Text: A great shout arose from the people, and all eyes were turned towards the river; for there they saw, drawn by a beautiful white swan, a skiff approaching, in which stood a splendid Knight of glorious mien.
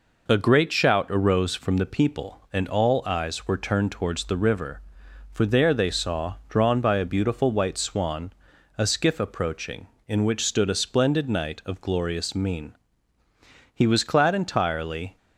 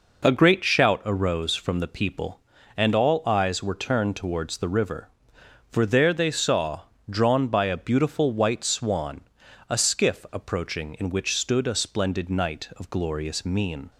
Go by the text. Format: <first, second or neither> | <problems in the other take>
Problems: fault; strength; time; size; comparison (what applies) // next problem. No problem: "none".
second | goes on to say "He was clad entirely"; from 13.7 s on; 1.4 s long